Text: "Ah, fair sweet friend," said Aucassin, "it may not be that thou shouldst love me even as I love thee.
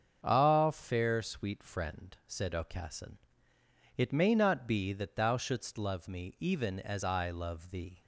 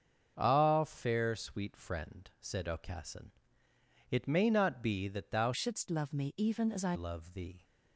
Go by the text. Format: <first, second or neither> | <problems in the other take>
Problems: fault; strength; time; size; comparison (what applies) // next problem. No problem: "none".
first | starts louder than the rest; until 1.3 s; 6.5 dB; also in the first // changes voice from "shouldst" to "I"; from 5.5 to 6.9 s; 1.4 s long